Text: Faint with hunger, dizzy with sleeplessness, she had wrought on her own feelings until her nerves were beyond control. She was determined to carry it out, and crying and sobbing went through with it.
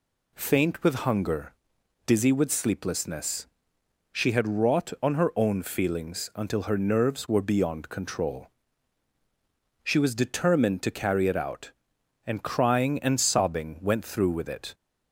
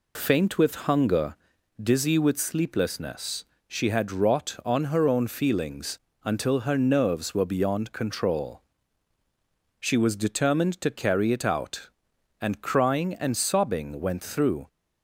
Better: first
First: none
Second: pauses between "feelings" and "until"; slight; at 5.9 s; 0.24 s long // stops before "with it"; at 14.6 s

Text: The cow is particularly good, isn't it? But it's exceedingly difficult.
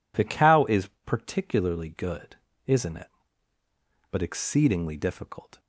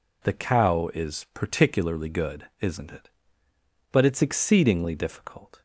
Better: second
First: pauses between "is" and "particularly"; slight; at 0.8 s; 0.18 s long // skips "it's"; at 4.2 s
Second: none

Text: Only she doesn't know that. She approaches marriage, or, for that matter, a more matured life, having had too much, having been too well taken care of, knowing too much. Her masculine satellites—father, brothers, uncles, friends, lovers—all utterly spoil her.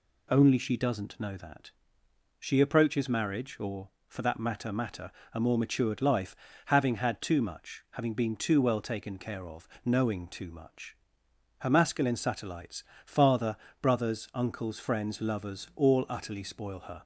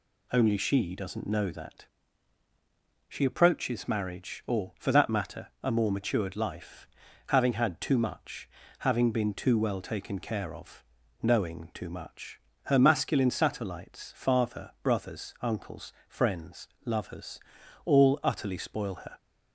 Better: second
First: says "matter" twice; at 4.7 s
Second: none

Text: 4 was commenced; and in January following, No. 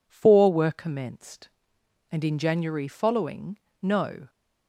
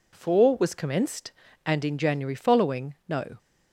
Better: second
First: says "were" for "was"; at 0.5 s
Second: none

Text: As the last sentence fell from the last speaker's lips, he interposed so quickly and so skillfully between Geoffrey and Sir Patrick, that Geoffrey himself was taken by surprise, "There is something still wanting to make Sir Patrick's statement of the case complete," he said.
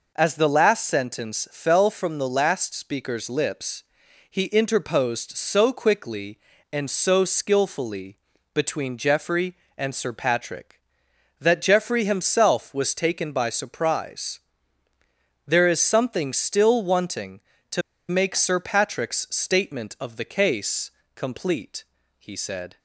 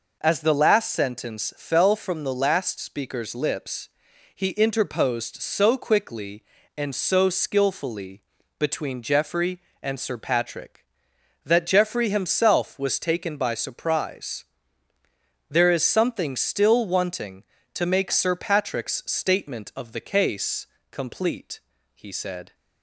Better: second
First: pauses between "skillfully" and "between"; slight; at 8.1 s; 0.36 s long // pauses between "to" and "make"; slight; at 17.8 s; 0.28 s long // pauses between "case" and "complete"; slight; at 20.9 s; 0.26 s long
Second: pauses between "skillfully" and "between"; slight; at 8.2 s; 0.36 s long // pauses between "case" and "complete"; slight; at 20.6 s; 0.26 s long

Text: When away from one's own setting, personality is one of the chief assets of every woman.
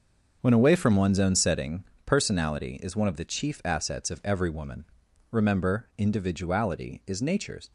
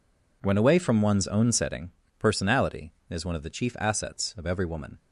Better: second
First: starts louder than the rest; until 1.4 s; 6.5 dB // goes on to say "Remember individuality is nature's"; strong; from 5.3 s on; 2.4 s long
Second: none

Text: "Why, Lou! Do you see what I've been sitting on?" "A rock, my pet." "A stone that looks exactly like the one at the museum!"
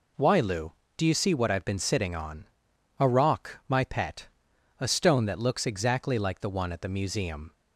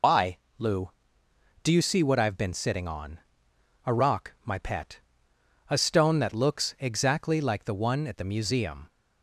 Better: first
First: none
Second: loses the start of "Why"; at 0.0 s; 115 ms

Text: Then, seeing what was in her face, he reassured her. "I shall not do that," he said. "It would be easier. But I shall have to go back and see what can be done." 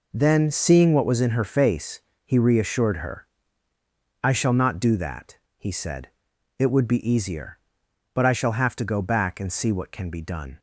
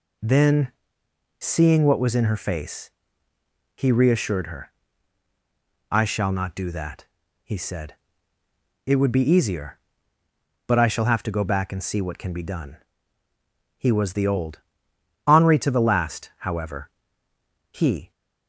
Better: first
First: none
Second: goes on to say "He was the old Henri to the last however He"; strong; from 13.7 s on; 4.3 s long

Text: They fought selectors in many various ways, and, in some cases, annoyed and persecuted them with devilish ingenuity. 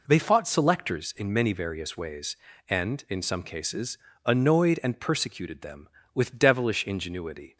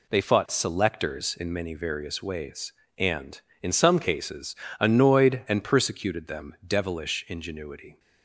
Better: first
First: none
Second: skips "with"; at 6.6 s

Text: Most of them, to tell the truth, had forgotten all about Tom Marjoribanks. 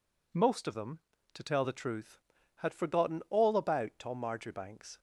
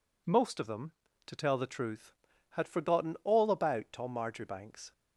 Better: neither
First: none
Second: none

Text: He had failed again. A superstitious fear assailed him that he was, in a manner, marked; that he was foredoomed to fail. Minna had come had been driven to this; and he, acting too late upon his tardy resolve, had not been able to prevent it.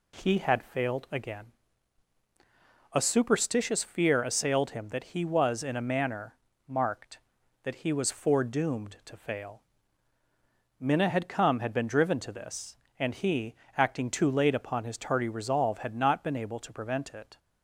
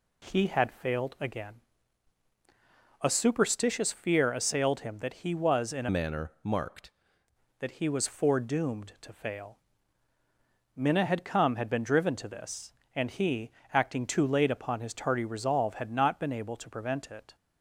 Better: first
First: none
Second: changes voice from "manner" to "marked"; from 5.8 to 6.9 s; 1.1 s long

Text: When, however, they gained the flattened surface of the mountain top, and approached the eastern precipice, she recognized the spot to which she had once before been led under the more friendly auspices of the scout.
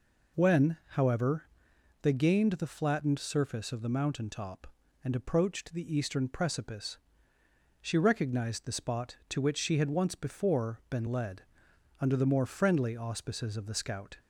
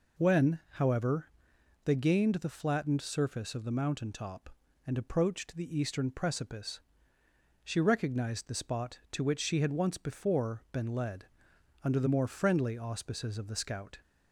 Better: neither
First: pauses between "led" and "under"; noticeable; at 11.4 s; 0.58 s long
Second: pauses between "led" and "under"; noticeable; at 11.2 s; 0.58 s long

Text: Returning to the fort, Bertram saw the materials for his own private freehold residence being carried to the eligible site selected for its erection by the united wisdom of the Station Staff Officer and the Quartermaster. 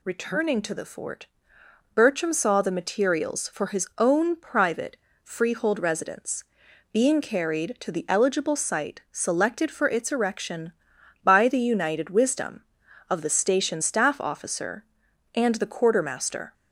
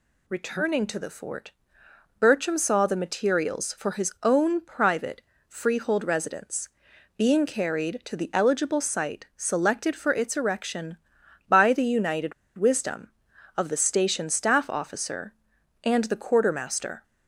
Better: first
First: pauses between "private" and "freehold"; slight; at 4.9 s; 0.28 s long // pauses between "residence" and "being"; noticeable; at 6.4 s; 0.48 s long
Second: pauses between "private" and "freehold"; slight; at 5.2 s; 0.28 s long // pauses between "residence" and "being"; noticeable; at 6.6 s; 0.48 s long // pauses between "united" and "wisdom"; slight; at 12.3 s; 0.23 s long

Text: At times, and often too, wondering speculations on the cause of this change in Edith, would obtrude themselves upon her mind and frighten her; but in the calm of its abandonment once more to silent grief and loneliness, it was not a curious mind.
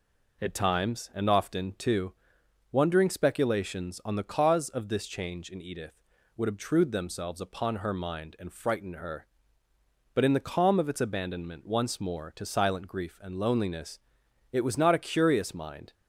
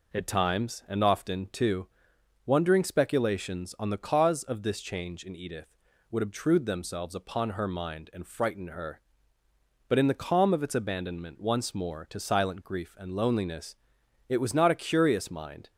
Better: neither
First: none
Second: none

